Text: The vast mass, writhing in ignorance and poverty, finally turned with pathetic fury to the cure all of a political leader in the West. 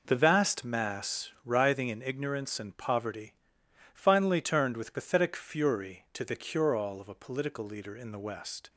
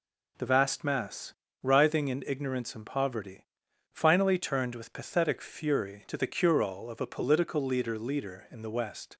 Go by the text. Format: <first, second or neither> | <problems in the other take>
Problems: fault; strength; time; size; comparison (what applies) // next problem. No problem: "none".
first | says "leader" twice; at 7.9 s